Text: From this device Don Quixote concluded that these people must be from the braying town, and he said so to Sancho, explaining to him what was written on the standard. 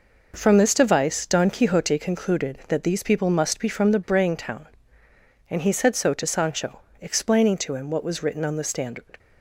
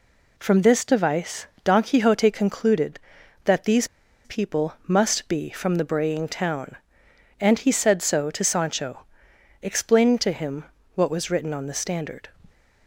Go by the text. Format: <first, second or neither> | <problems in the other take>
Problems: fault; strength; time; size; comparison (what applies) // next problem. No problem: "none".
first | pauses between "device" and "Don"; slight; at 1.4 s; 0.16 s long // pauses between "these" and "people"; at 3.8 s; 0.36 s long // pauses between "him" and "what"; slight; at 10.6 s; 0.32 s long